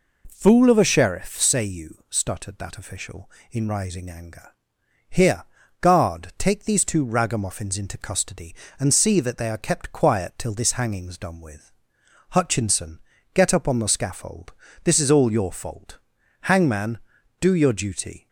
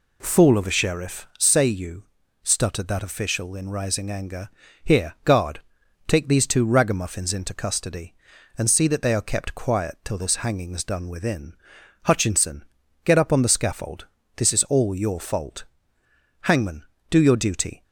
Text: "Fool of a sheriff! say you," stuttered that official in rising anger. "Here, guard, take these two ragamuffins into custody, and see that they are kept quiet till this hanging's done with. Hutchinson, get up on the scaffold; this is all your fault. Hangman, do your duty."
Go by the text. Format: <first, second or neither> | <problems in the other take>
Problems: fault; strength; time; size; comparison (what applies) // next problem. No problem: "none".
first | says "within" for "with"; at 11.0 s